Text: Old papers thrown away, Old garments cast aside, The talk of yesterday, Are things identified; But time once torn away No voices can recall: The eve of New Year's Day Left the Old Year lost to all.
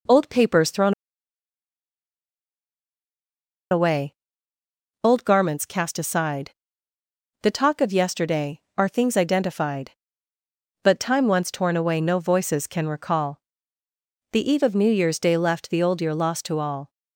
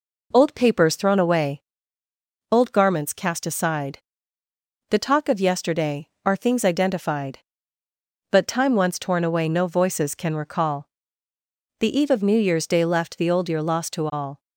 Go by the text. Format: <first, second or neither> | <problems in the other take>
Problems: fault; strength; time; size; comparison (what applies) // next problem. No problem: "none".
second | pauses between "thrown" and "away"; strong; at 0.9 s; 2.7 s long